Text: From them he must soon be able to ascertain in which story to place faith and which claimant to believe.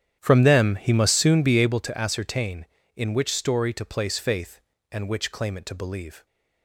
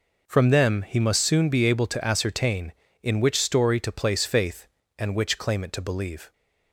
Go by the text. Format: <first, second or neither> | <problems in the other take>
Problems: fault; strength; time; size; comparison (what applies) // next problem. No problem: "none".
second | starts louder than the rest; strong; until 1.9 s; 9.5 dB